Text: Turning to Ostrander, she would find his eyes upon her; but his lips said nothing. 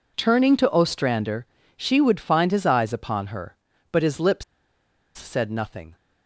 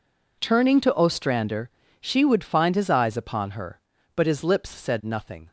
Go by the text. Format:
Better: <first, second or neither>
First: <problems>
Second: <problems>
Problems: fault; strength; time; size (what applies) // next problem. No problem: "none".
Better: second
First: pauses between "lips" and "said"; noticeable; at 4.4 s; 0.71 s long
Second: none